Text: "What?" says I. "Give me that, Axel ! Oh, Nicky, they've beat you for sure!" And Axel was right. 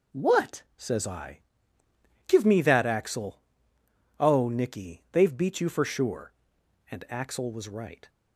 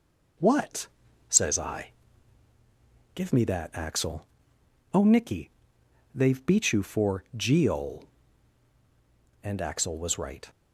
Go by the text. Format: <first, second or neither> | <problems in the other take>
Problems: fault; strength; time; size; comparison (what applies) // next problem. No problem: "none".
first | says "geol" for "sure"; at 7.3 s